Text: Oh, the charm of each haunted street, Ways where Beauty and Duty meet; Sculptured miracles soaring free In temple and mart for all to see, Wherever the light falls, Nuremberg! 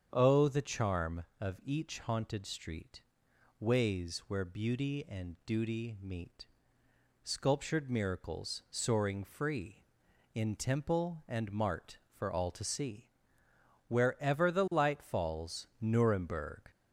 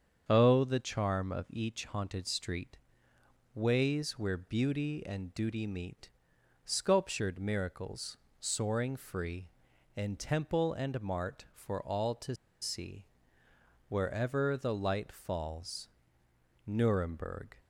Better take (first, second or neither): first